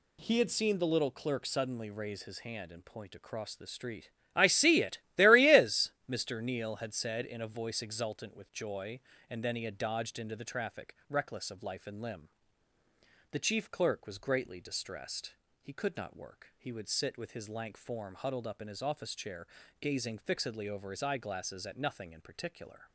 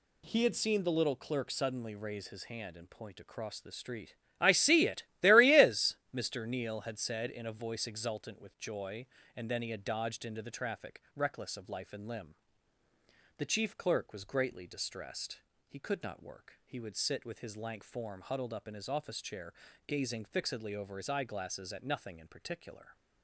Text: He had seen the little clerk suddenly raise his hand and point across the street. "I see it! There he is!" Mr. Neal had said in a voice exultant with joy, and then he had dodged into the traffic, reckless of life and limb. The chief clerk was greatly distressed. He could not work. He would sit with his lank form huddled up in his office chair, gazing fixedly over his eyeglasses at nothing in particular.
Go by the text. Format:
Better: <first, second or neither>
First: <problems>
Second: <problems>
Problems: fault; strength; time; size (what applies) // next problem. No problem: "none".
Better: neither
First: none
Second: none